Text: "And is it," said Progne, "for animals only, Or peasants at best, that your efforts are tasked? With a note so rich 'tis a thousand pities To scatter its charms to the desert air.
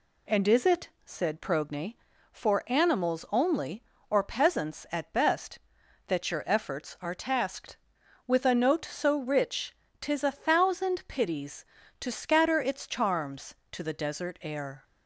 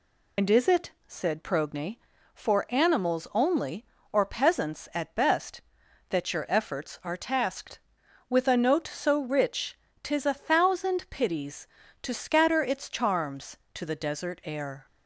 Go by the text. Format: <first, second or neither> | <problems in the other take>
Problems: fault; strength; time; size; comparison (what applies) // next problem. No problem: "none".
first | loses the start of "And"; at 0.3 s; 85 ms // pauses between "rich" and "tis"; slight; at 9.7 s; 0.28 s long; slight in the first